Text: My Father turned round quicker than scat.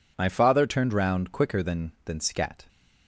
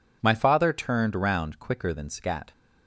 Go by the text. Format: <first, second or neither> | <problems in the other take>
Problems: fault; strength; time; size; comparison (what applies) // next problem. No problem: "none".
second | says "than" twice; at 2.0 s